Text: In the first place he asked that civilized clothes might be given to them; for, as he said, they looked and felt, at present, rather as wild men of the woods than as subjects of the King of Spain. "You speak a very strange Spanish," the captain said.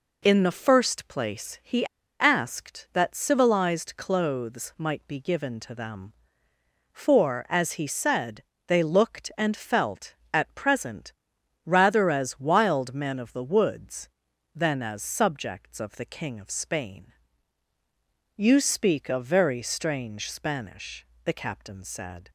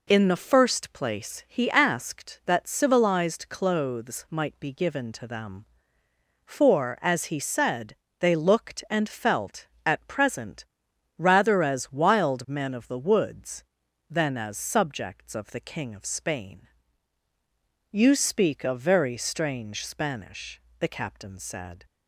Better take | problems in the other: second | pauses between "he" and "asked"; slight; at 1.8 s; 0.34 s long

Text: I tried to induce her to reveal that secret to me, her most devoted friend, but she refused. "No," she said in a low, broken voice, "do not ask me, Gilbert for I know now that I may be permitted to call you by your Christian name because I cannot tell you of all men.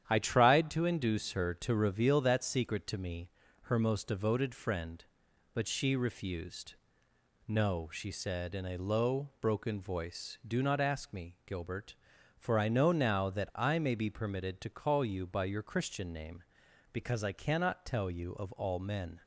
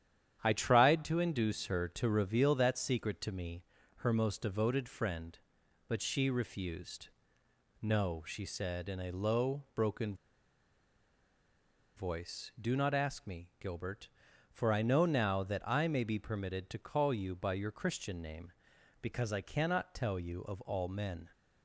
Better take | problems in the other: first | starts louder than the rest; strong; until 1.4 s; 9.5 dB; strong in the first // pauses between "broken" and "voice"; strong; at 10.1 s; 1.8 s long

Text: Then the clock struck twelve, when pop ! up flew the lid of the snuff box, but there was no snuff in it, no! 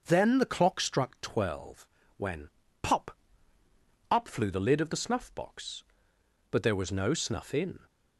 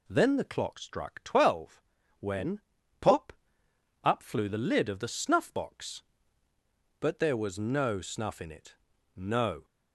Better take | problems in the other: second | pauses between "when" and "pop"; slight; at 2.5 s; 0.32 s long; also in the second // stops before "it no"; at 7.8 s

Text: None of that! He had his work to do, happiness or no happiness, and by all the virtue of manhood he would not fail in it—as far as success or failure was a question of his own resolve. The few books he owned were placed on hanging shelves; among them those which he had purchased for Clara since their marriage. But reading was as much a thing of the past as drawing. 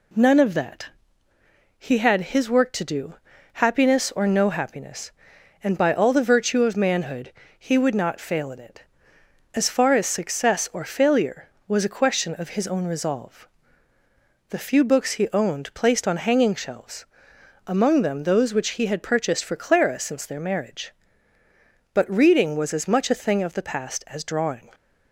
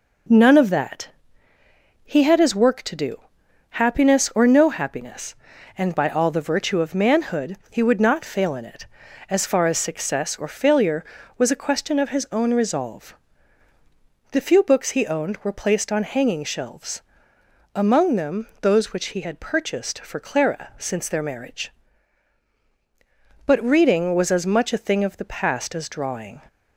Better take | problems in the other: second | pauses between "manhood" and "he"; slight; at 7.3 s; 0.26 s long; slight in the second // skips "were"; at 15.7 s

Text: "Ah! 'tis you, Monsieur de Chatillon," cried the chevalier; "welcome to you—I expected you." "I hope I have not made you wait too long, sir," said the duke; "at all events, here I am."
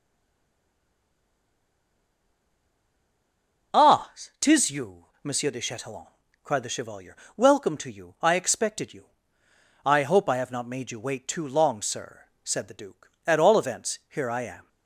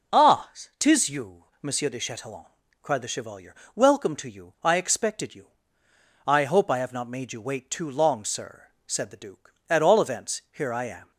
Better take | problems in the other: second | stays silent before the first word; strong; until 3.7 s; 3.7 s long

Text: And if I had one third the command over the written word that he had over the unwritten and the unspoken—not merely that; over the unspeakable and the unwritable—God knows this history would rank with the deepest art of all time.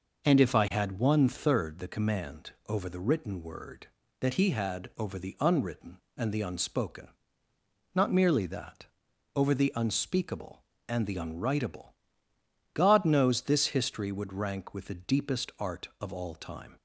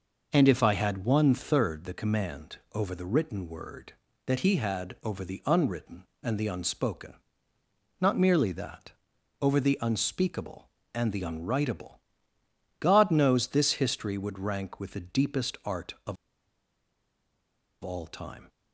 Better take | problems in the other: first | pauses between "command" and "over"; slight; at 2.5 s; 0.16 s long; slight in the first // pauses between "of" and "all"; strong; at 16.1 s; 1.6 s long

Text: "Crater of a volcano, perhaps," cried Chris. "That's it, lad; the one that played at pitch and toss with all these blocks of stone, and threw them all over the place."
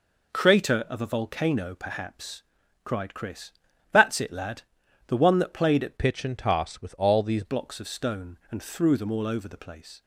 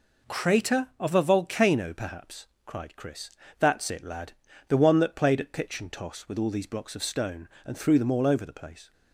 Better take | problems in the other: second | changes voice from "pitch" to "these"; from 5.9 to 7.4 s; 1.5 s long

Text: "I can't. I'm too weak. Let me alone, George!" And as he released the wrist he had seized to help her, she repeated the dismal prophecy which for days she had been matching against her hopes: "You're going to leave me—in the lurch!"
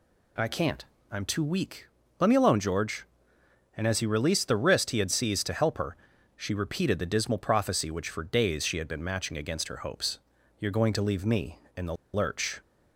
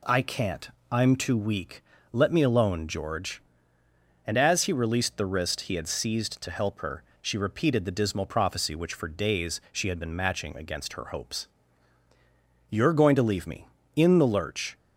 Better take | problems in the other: second | pauses between "the" and "lurch"; slight; at 11.9 s; 0.18 s long

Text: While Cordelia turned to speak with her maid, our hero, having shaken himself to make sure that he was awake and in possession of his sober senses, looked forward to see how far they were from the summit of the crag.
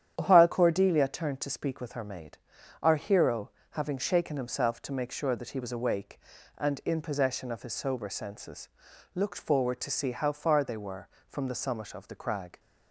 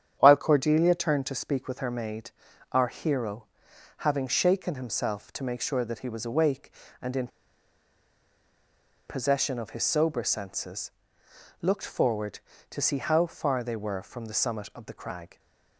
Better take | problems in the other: first | starts louder than the rest; strong; until 1.1 s; 9 dB; strong in the first // pauses between "in" and "possession"; strong; at 7.2 s; 1.7 s long

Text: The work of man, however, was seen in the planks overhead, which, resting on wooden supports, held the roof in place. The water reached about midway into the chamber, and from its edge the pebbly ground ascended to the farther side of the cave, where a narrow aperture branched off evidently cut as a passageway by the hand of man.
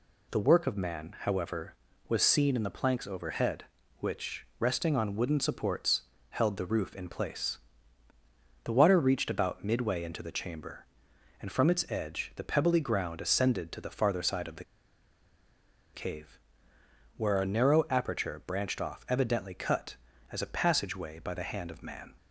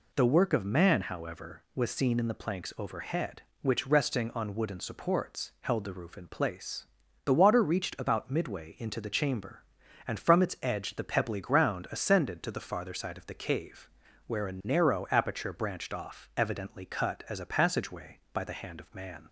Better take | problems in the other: second | pauses between "the" and "cave"; strong; at 14.6 s; 1.3 s long

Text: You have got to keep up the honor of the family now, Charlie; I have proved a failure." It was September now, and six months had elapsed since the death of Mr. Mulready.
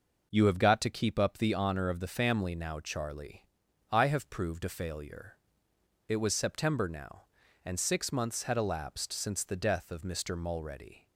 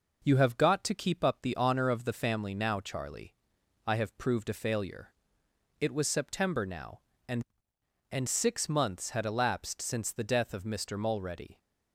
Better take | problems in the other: first | says "and" twice; at 8.0 s

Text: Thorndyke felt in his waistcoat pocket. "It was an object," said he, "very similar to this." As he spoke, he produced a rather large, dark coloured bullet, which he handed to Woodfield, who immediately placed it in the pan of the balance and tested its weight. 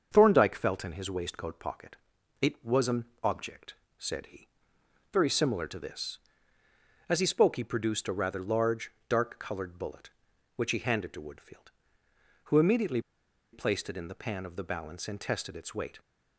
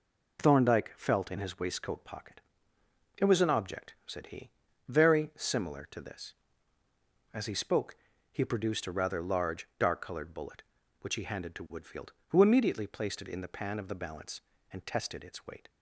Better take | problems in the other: second | starts louder than the rest; until 1.1 s; 6.5 dB // pauses between "an" and "object"; slight; at 3.0 s; 0.16 s long // pauses between "immediately" and "placed"; noticeable; at 13.0 s; 0.52 s long

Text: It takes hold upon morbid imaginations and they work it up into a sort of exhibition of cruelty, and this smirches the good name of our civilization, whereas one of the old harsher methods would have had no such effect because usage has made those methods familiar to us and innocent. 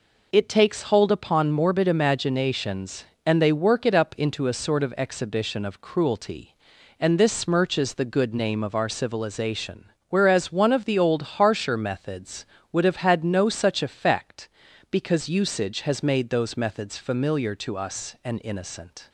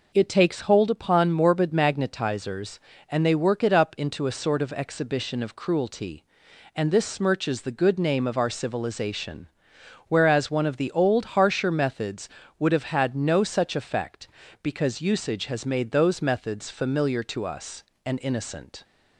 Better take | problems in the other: first | says "magnetizers" for "imaginations"; at 1.7 s

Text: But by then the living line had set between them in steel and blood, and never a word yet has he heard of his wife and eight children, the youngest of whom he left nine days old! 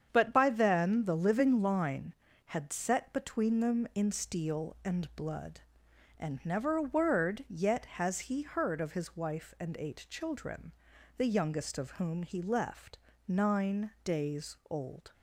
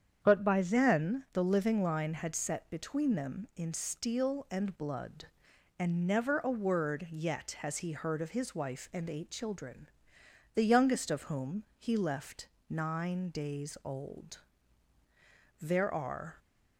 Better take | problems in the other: first | starts louder than the rest; strong; until 1.2 s; 8 dB; strong in the first // pauses between "left" and "nine"; slight; at 12.4 s; 0.22 s long; slight in the first // goes on to say "There are"; noticeable; from 15.6 s on; 0.76 s long

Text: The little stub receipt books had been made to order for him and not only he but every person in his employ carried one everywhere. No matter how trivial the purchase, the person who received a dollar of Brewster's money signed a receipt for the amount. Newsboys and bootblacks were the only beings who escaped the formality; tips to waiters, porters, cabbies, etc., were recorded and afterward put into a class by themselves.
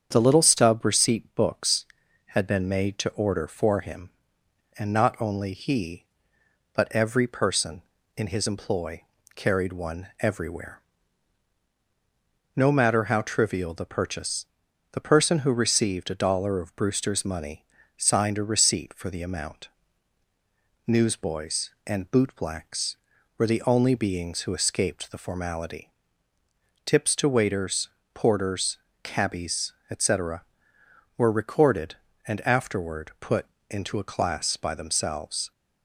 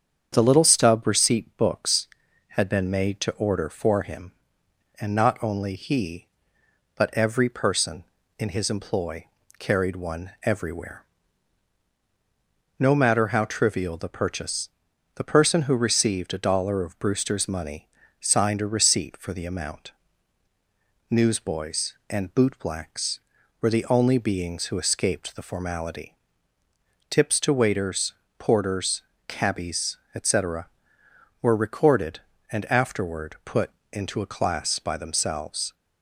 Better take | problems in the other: neither | starts louder than the rest; strong; the same in both // pauses between "employ" and "carried"; slight; the same in both // pauses between "money" and "signed"; slight; the same in both // pauses between "put" and "into"; slight; the same in both

